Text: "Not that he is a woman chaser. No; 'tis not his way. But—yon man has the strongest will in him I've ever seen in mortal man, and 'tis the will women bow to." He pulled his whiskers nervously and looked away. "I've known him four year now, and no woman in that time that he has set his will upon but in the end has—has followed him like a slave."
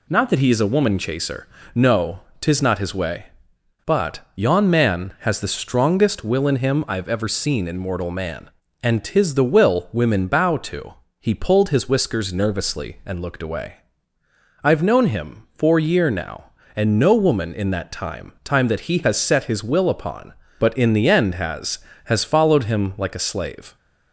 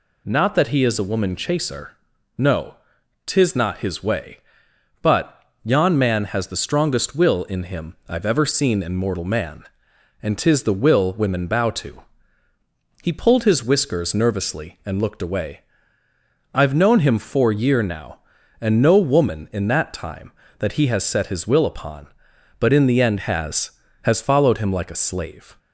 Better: second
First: says "time" twice; at 18.4 s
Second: none

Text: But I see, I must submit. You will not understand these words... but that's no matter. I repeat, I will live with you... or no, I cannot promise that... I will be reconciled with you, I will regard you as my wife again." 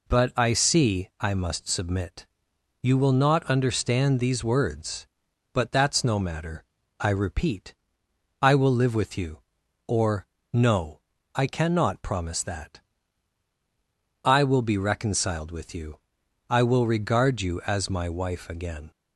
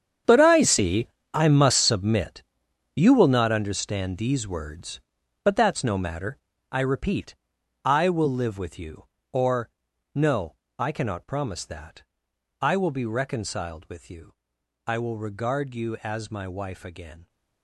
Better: first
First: pauses between "or" and "no"; slight; at 10.2 s; 0.28 s long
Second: gets quieter; strong; throughout; 15 dB // pauses between "or" and "no"; noticeable; at 9.6 s; 0.46 s long

